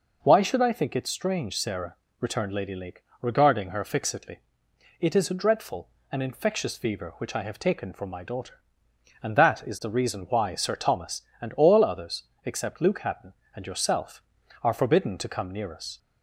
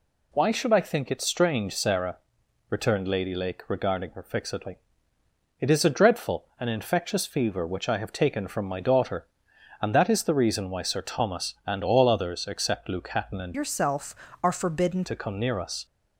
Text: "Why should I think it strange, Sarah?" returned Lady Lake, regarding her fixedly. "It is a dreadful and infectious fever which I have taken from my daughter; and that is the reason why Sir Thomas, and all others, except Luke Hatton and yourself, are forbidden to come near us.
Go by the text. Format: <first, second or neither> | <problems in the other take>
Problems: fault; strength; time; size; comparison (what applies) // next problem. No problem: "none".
first | changes voice from "yourself" to "forbidden"; from 13.5 to 15.0 s; 1.5 s long